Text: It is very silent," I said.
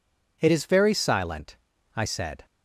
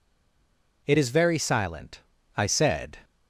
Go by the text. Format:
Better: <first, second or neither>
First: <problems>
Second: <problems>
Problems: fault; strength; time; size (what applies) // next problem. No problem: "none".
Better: first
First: none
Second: stays silent before the first word; slight; until 0.8 s; 0.8 s long